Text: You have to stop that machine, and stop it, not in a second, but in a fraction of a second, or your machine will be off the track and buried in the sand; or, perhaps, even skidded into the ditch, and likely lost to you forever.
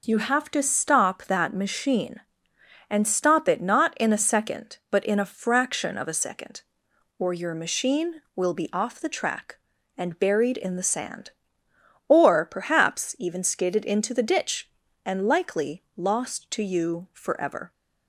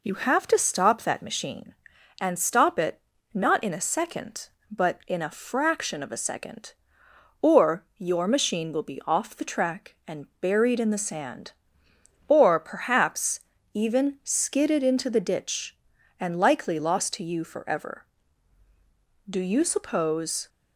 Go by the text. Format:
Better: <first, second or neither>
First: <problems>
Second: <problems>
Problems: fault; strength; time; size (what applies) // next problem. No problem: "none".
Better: first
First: none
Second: goes on to say "Do you suppose"; noticeable; from 19.2 s on; 1.2 s long